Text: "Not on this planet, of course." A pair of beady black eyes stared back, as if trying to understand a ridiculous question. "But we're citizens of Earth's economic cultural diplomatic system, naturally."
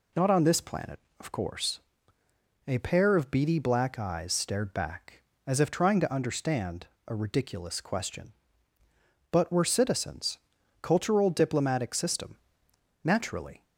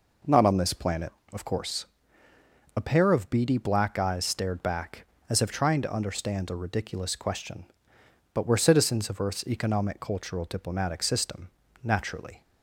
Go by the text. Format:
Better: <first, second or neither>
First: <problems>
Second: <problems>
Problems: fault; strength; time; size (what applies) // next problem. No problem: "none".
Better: second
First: pauses between "understand" and "a"; slight; at 6.8 s; 0.20 s long // skips "of Earth's economic"; at 10.5 s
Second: none